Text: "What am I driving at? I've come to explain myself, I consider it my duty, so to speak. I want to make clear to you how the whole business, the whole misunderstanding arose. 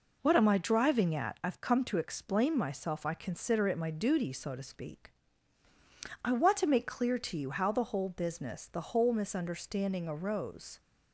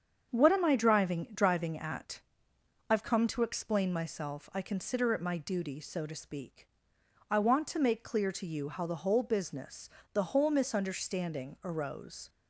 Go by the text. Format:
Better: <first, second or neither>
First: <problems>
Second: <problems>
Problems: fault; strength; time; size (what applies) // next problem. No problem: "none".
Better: first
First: none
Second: starts louder than the rest; strong; until 1.3 s; 7.5 dB // says "driving" twice; at 1.3 s